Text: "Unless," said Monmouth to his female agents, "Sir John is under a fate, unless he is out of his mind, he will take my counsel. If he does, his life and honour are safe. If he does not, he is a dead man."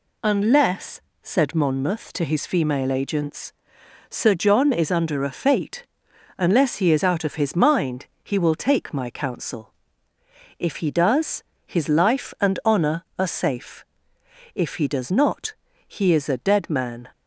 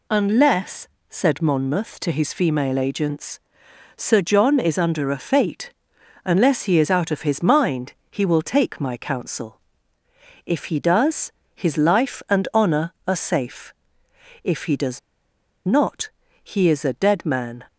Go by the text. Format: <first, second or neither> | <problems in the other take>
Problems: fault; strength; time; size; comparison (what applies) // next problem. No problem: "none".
first | pauses between "does" and "not"; noticeable; at 14.9 s; 0.67 s long